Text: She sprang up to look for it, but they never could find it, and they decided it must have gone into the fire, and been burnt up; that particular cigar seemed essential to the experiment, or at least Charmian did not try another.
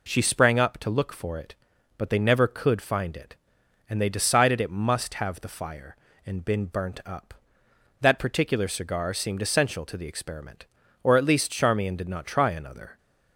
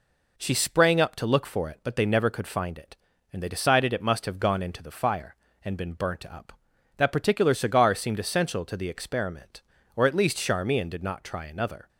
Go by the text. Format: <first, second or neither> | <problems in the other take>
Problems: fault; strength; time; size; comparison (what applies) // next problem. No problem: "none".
second | skips "gone into"; at 5.4 s